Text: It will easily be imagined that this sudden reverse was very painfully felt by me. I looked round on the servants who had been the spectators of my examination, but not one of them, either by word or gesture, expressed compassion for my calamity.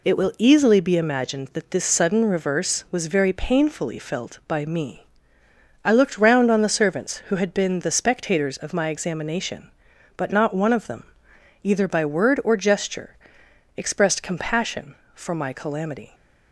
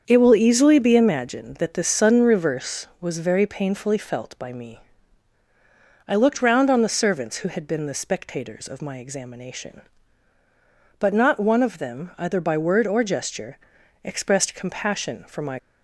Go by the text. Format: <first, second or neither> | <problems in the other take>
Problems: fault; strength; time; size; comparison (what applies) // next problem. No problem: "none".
first | starts louder than the rest; strong; until 1.0 s; 7 dB // stops before "calamity"; at 15.5 s